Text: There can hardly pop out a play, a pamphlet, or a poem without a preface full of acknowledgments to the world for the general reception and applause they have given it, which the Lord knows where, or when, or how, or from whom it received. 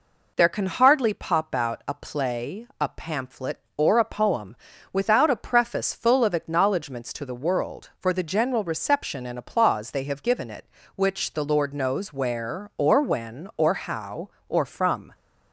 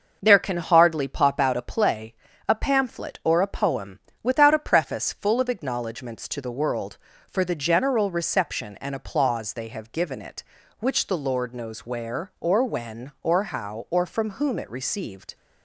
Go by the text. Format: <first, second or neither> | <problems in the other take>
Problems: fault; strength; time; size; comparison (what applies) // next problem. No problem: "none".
second | pauses between "poem" and "without"; slight; at 4.5 s; 0.36 s long; slight in the second // stops before "whom it received"; at 15.1 s